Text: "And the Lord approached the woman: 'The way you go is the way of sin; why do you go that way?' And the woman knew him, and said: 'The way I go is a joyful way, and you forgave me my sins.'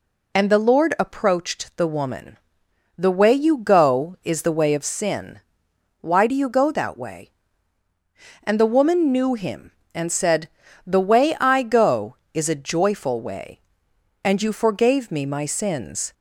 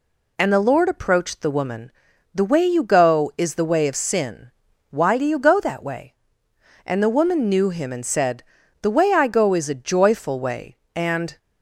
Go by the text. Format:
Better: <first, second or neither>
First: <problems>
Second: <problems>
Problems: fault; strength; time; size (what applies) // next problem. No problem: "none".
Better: first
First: none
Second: stops before "you forgave me my sins"; at 11.3 s